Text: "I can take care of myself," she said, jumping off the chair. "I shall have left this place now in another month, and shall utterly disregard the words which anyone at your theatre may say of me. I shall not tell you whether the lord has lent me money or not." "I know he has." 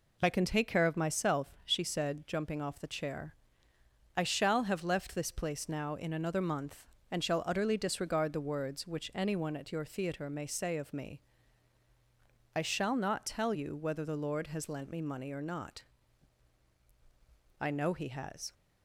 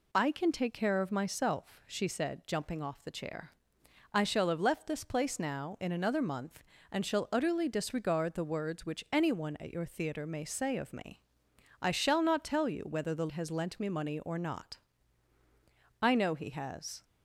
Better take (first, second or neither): first